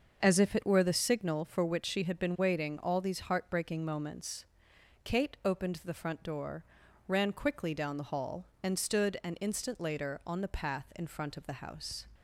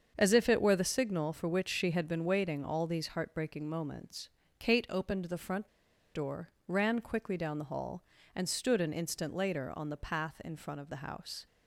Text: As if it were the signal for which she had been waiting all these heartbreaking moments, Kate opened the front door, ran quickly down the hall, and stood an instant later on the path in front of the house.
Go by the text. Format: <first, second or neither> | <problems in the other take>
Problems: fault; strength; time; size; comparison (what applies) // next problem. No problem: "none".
first | starts louder than the rest; until 1.1 s; 7 dB; also in the first // pauses between "front" and "door"; noticeable; at 5.6 s; 0.46 s long